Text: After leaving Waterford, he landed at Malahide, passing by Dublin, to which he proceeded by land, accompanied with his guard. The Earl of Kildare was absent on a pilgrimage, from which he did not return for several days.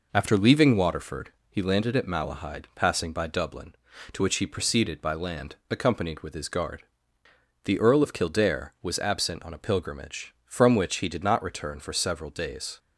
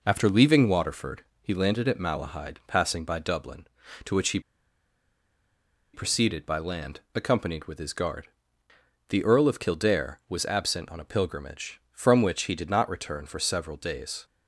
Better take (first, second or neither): first